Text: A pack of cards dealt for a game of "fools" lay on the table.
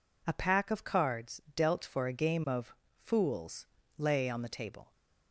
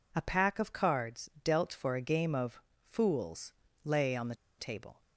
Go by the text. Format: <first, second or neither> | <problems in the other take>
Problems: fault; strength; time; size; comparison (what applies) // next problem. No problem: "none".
first | pauses between "of" and "fools"; slight; at 2.6 s; 0.24 s long; slight in the first // pauses between "fools" and "lay"; slight; at 3.5 s; 0.28 s long; slight in the first // pauses between "the" and "table"; slight; at 4.3 s; 0.24 s long